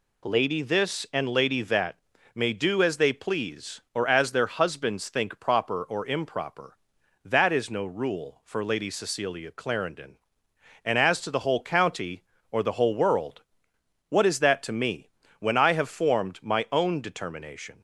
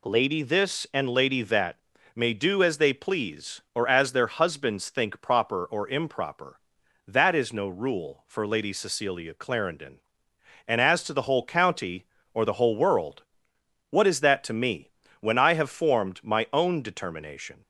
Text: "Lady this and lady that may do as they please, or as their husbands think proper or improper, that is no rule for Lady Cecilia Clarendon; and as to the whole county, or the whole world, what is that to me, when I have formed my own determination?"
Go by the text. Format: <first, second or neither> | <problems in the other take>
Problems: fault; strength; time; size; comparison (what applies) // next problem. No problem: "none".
neither | pauses between "that" and "may"; slight; the same in both